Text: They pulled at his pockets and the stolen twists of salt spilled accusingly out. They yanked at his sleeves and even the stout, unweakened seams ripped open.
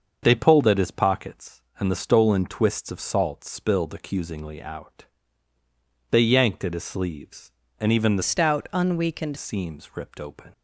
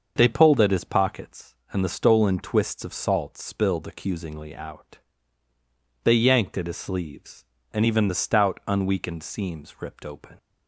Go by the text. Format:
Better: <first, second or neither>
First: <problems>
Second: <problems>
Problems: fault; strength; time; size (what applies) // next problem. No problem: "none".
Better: second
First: starts louder than the rest; until 1.2 s; 6.5 dB // changes voice from "stout" to "unweakened"; from 8.2 to 9.3 s; 1.1 s long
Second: starts louder than the rest; until 1.1 s; 6.5 dB